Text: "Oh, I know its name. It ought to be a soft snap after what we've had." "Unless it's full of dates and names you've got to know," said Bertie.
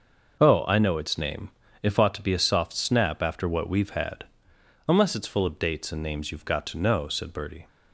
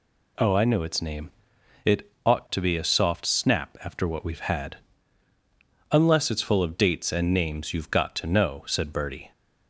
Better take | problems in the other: second | says "If" for "It"; at 1.8 s

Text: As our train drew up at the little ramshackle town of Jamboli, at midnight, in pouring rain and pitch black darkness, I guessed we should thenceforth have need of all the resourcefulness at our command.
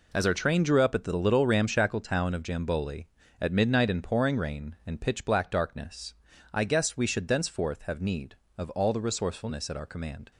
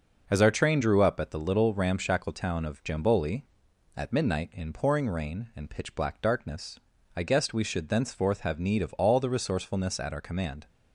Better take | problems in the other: neither | none

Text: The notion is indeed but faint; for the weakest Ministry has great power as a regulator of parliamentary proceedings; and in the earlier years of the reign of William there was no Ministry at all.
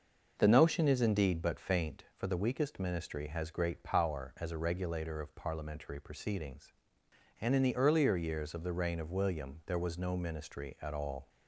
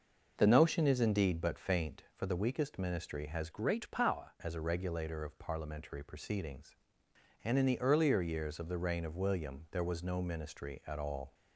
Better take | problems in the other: first | changes voice from "great" to "power"; from 3.5 to 4.3 s; 0.8 s long

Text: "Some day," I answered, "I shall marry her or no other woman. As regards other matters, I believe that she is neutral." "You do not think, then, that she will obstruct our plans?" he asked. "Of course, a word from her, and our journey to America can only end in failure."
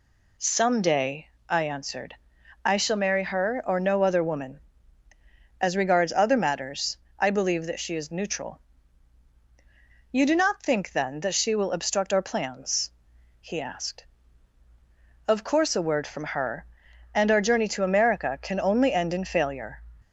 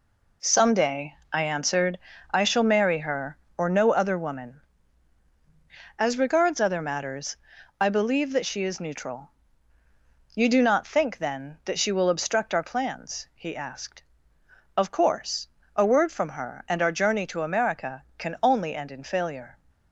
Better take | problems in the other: neither | none

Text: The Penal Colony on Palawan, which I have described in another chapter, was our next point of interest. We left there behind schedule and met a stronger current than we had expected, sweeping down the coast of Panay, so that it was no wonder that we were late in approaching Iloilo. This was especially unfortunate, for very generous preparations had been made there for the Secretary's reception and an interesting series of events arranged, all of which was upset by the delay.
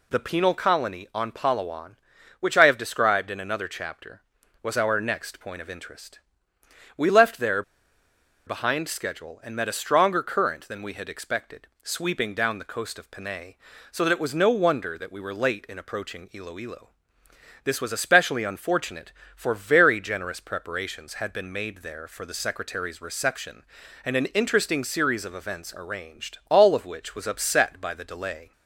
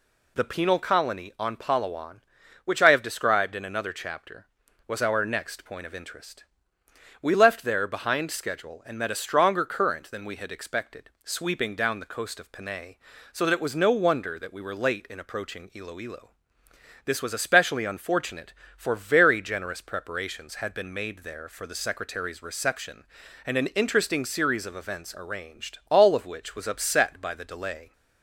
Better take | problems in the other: second | pauses between "there" and "behind"; noticeable; at 7.6 s; 0.84 s long

